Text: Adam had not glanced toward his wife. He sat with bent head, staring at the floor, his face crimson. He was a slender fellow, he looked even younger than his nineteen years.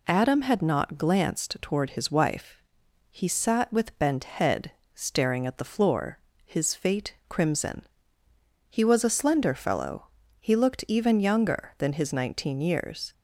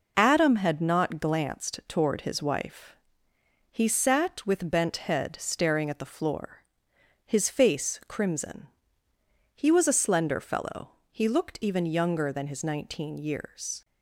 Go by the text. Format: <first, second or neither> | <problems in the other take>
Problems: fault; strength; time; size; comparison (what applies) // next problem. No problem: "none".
second | says "fate" for "face"; at 6.7 s